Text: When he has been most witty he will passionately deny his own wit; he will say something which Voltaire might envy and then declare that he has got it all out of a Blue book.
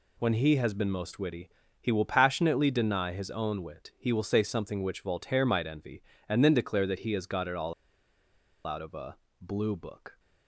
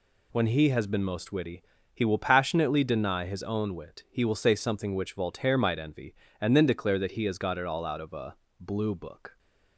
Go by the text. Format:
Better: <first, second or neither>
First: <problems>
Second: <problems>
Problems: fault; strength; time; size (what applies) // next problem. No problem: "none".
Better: second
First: pauses between "witty" and "he"; slight; at 1.4 s; 0.32 s long // pauses between "all" and "out"; noticeable; at 7.7 s; 0.93 s long // pauses between "a" and "Blue"; slight; at 9.1 s; 0.24 s long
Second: pauses between "witty" and "he"; slight; at 1.6 s; 0.32 s long // pauses between "a" and "Blue"; slight; at 8.3 s; 0.24 s long